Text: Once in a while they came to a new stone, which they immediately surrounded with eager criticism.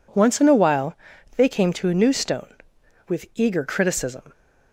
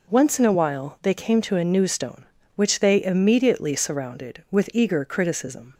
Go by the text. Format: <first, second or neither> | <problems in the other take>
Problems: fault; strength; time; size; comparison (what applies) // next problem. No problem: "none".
second | pauses between "while" and "they"; at 0.9 s; 0.42 s long // skips "which they immediately surrounded"; at 2.8 s